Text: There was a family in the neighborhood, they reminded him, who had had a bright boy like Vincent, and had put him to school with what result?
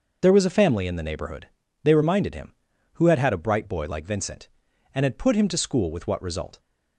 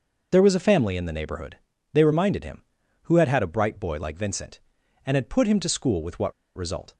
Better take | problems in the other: first | pauses between "what" and "result"; slight; at 6.3 s; 0.23 s long

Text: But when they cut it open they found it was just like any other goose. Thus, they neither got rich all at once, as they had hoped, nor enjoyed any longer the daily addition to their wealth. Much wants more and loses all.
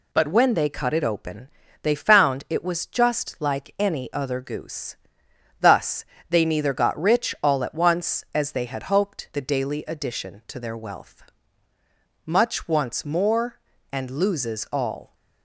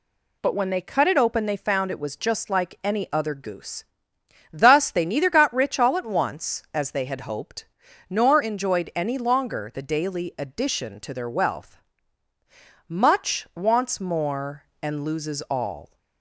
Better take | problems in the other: second | pauses between "open" and "they"; slight; at 1.4 s; 0.36 s long // skips "nor enjoyed any longer"; at 9.3 s

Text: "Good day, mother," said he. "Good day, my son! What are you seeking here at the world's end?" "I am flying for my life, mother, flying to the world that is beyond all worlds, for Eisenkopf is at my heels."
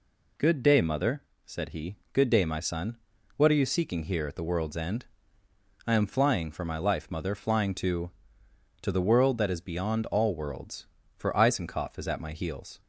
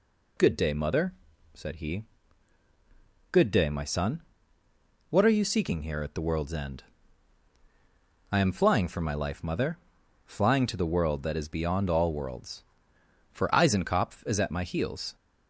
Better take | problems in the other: second | says "to" twice; at 8.8 s

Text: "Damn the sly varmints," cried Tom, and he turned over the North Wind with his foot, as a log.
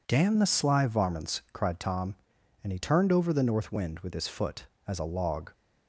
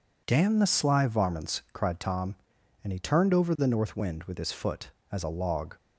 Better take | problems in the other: neither | none

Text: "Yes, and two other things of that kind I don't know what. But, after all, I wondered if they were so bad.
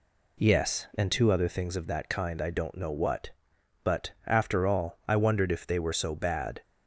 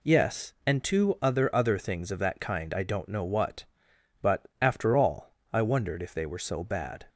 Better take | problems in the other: first | says "other" twice; at 1.5 s

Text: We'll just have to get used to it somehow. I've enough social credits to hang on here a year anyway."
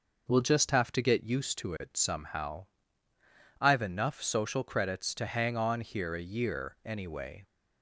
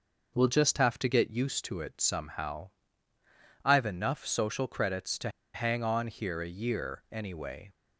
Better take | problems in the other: first | pauses between "to" and "hang"; slight; at 5.2 s; 0.25 s long

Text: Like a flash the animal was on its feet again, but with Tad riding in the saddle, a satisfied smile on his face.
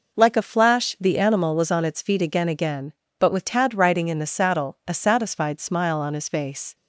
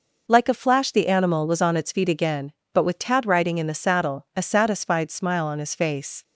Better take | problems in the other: second | says "again" twice; at 2.4 s

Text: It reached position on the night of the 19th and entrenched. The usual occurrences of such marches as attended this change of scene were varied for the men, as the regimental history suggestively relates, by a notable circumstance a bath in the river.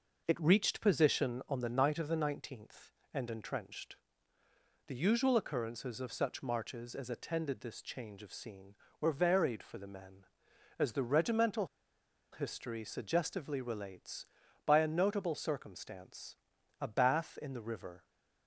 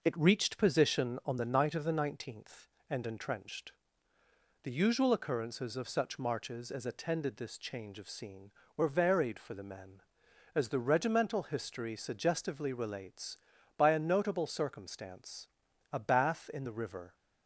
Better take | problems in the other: second | pauses between "regimental" and "history"; noticeable; at 11.6 s; 0.64 s long // pauses between "circumstance" and "a"; at 16.3 s; 0.44 s long; also in the second

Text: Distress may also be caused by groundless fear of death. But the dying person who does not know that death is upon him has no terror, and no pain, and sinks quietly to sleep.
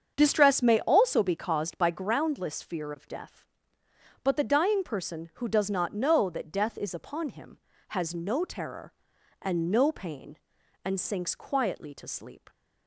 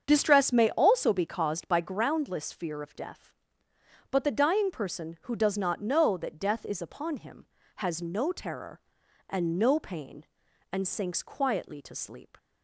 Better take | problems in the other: neither | starts louder than the rest; the same in both

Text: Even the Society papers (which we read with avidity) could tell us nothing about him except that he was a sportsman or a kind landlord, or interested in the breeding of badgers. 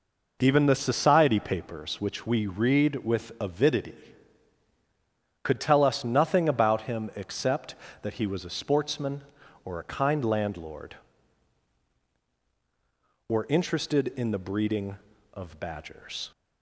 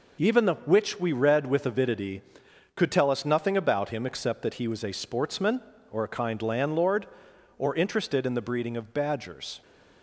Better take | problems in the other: first | skips "Society papers"; at 0.5 s

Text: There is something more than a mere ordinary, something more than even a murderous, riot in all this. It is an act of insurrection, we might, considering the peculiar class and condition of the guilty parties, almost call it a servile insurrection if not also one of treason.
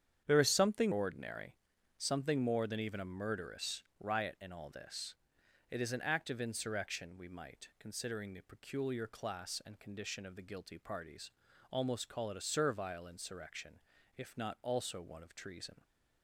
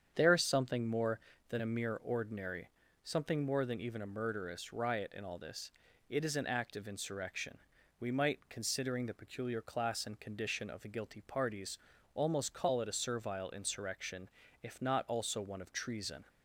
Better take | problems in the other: second | starts louder than the rest; strong; until 1.2 s; 8.5 dB; strong in the second // skips "more than a mere"; at 0.9 s // pauses between "insurrection" and "if"; slight; at 13.8 s; 0.34 s long; slight in the second

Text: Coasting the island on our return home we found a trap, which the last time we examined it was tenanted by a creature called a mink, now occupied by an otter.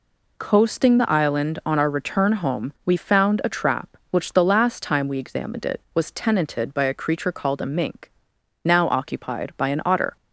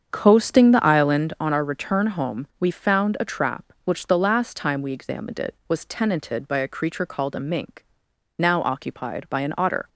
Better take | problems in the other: first | starts louder than the rest; strong; until 1.4 s; 7.5 dB

